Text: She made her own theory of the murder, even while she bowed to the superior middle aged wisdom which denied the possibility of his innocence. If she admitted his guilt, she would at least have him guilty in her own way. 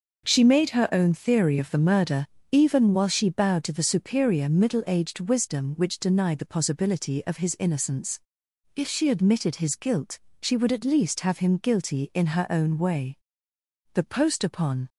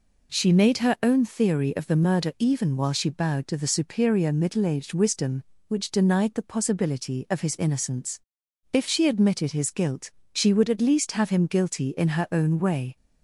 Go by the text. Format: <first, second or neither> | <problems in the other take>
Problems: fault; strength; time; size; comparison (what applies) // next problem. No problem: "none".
second | goes on to say "The post upon"; noticeable; from 13.9 s on; 0.96 s long